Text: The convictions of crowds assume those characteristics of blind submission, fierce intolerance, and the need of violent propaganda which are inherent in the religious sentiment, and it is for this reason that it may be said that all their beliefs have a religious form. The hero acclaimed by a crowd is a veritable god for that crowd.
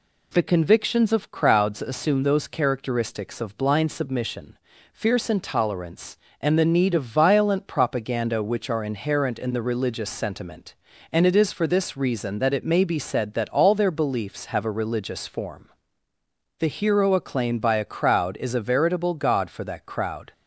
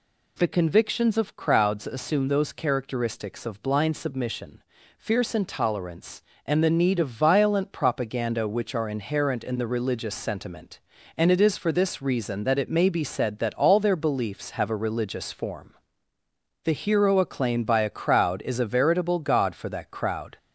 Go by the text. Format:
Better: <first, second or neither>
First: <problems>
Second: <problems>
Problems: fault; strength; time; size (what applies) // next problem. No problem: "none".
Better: first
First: none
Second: gets louder; slight; throughout; 2.5 dB